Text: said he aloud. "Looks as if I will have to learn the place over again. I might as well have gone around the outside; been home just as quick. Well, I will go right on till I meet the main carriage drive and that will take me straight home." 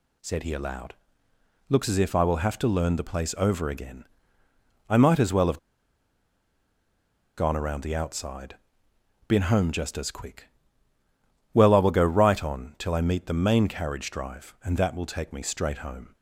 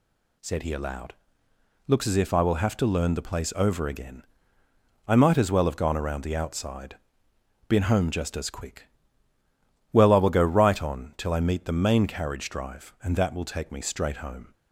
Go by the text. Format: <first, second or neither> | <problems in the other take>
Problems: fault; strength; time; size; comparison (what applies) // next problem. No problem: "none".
second | pauses between "have" and "gone"; strong; at 5.5 s; 1.7 s long